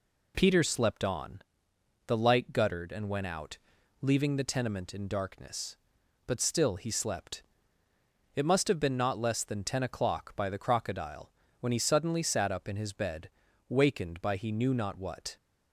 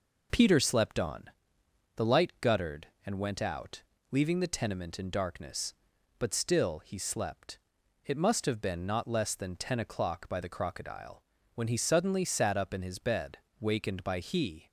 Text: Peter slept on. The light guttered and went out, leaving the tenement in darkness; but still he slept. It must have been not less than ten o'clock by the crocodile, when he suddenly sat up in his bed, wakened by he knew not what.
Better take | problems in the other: first | stops before "knew not what"; at 14.6 s

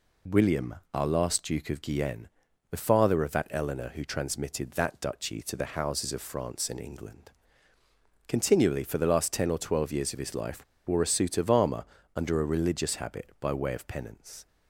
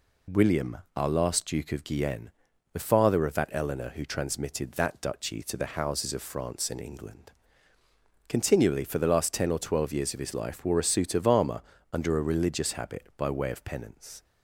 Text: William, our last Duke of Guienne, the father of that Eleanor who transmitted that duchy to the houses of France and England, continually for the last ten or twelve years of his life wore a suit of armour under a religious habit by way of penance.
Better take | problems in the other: second | pauses between "life" and "wore"; slight; at 10.6 s; 0.22 s long // pauses between "armour" and "under"; slight; at 11.8 s; 0.30 s long; slight in the second

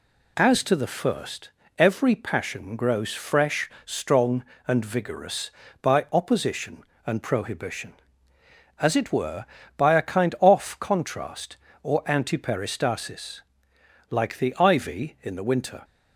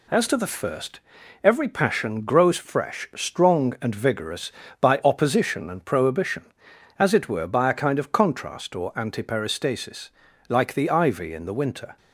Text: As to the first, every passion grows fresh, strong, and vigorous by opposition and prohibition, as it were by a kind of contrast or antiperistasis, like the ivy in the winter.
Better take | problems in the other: second | says "off" for "of"; at 10.3 s

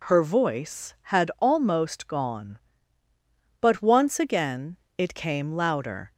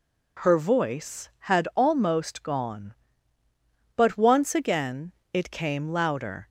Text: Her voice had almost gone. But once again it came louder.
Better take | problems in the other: neither | pauses between "again" and "it"; slight; the same in both

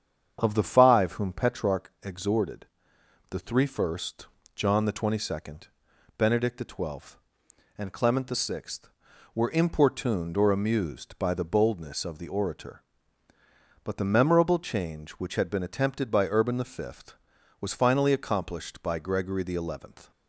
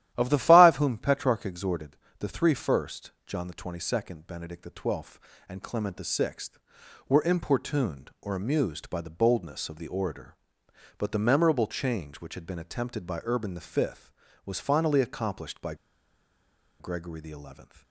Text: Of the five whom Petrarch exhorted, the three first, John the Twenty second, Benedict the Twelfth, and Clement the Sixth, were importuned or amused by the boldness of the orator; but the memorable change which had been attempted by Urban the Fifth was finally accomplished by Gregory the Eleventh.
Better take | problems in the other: first | starts louder than the rest; strong; until 1.1 s; 12.5 dB; strong in the first // pauses between "by" and "Gregory"; at 15.7 s; 1.0 s long

